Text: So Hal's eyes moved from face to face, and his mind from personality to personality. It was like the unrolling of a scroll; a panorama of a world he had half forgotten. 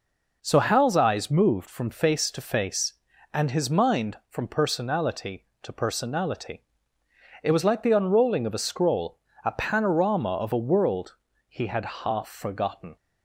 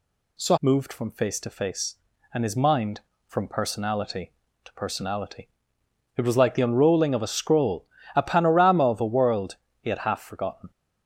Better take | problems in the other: first | skips "Hal's eyes"; at 0.5 s // pauses between "world" and "he"; slight; at 9.5 s; 0.26 s long; slight in the first

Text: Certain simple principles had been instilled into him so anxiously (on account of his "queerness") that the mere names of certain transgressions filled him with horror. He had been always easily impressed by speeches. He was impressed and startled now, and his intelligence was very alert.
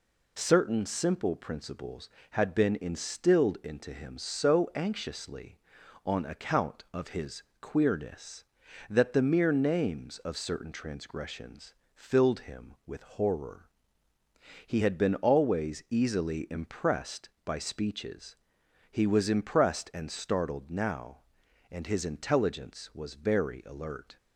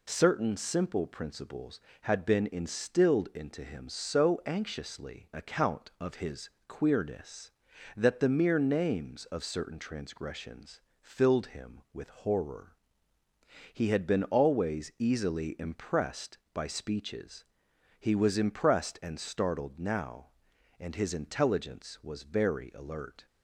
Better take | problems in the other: first | skips "on"; at 5.3 s // pauses between "his" and "queerness"; slight; at 6.4 s; 0.18 s long; slight in the first // pauses between "transgressions" and "filled"; slight; at 10.7 s; 0.22 s long; slight in the first

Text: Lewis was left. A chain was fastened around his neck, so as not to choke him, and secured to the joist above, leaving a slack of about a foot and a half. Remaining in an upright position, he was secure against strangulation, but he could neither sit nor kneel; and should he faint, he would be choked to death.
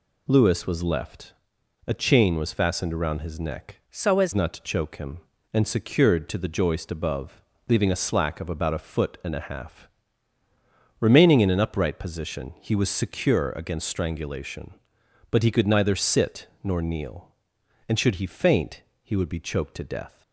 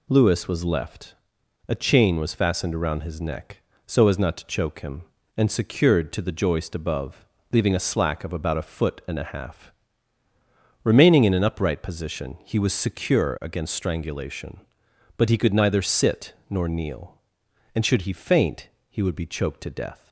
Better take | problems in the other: second | changes voice from "so" to "as"; from 3.8 to 4.3 s; 0.5 s long // pauses between "sit" and "nor"; slight; at 16.4 s; 0.16 s long; slight in the second

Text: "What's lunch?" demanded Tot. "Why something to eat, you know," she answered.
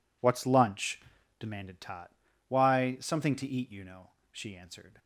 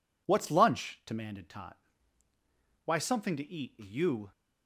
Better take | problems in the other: first | stops before "know she answered"; at 4.3 s

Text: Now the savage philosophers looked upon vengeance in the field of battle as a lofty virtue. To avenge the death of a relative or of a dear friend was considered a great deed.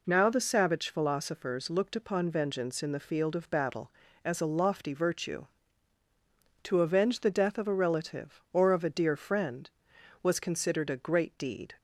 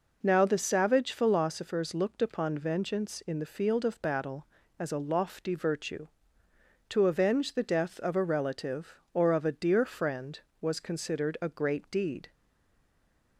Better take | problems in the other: first | stays silent after the last word; from 12.3 s on; 1.0 s long

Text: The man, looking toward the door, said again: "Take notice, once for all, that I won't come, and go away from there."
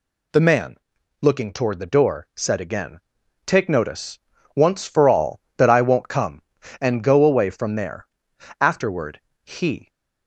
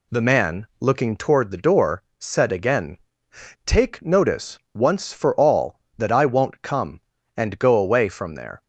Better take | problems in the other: second | goes on to say "Afterward he"; noticeable; from 8.6 s on; 1.2 s long

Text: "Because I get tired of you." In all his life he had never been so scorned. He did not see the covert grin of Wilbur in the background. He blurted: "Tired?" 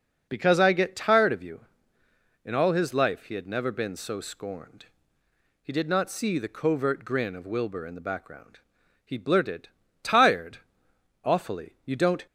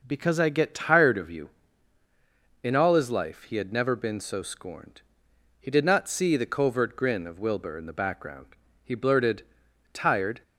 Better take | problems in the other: second | goes on to say "Awfully You don't"; noticeable; from 11.2 s on; 1.0 s long

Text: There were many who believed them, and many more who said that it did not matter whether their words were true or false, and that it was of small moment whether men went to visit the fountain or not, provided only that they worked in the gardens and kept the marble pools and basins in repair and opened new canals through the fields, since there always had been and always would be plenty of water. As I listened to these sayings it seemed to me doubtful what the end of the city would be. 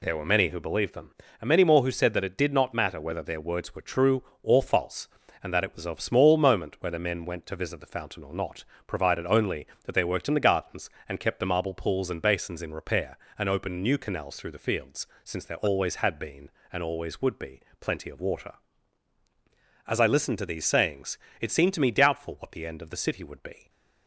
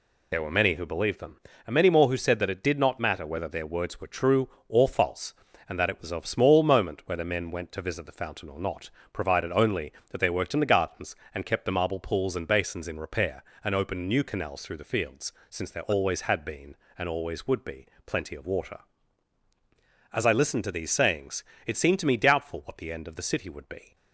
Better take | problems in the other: first | loses the start of "There"; at 0.3 s; 40 ms // pauses between "be" and "plenty"; slight; at 17.8 s; 0.18 s long; slight in the first // pauses between "sayings" and "it"; slight; at 21.4 s; 0.22 s long; slight in the first

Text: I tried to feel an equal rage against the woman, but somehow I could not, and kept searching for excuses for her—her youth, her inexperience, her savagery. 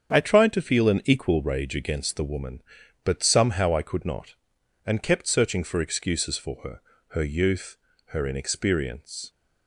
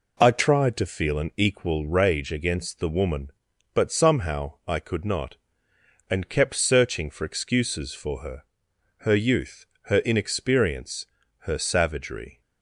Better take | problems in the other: second | starts louder than the rest; strong; until 1.1 s; 7.5 dB // stops before "her savagery"; at 9.2 s

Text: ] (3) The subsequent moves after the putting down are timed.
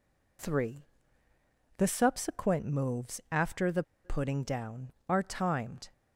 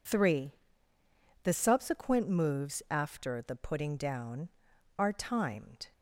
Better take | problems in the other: second | pauses between "the" and "putting"; slight; at 3.8 s; 0.22 s long

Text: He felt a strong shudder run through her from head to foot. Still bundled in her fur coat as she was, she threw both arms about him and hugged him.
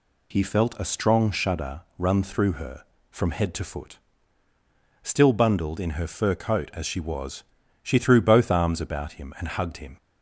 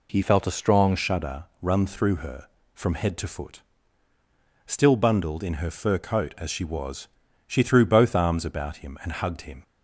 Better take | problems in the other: first | changes voice from "felt" to "strong"; from 0.2 to 0.9 s; 0.7 s long // pauses between "shudder" and "run"; slight; at 1.4 s; 0.16 s long; slight in the first

